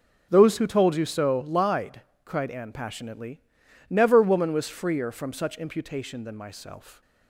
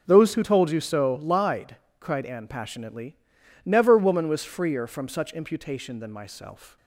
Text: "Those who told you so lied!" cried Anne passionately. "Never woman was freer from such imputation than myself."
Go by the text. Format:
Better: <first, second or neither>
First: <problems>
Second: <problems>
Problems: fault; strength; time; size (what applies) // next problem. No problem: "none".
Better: neither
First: none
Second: none